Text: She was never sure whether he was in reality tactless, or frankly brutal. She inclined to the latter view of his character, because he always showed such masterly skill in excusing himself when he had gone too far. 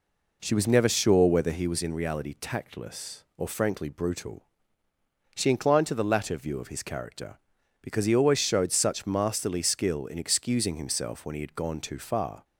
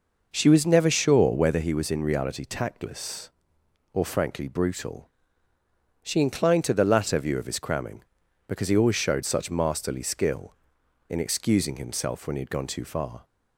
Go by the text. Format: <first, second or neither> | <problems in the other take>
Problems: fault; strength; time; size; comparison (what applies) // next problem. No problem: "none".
first | says "cramming" for "character"; at 7.5 s